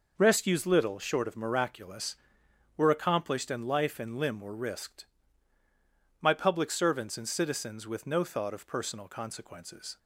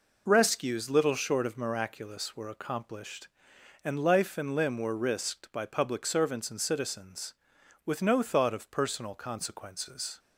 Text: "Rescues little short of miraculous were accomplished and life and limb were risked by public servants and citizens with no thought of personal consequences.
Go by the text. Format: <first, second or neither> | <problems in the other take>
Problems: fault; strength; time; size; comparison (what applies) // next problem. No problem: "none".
second | says "my" for "by"; at 6.1 s